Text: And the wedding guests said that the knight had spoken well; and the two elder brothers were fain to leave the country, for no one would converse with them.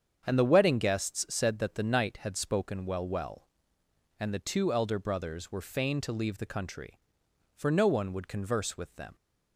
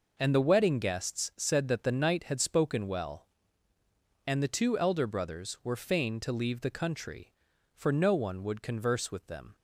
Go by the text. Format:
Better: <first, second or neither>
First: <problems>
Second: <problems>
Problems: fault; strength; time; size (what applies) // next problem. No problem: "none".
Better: second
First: starts louder than the rest; strong; until 1.2 s; 7.5 dB // says "well" twice; at 3.0 s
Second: none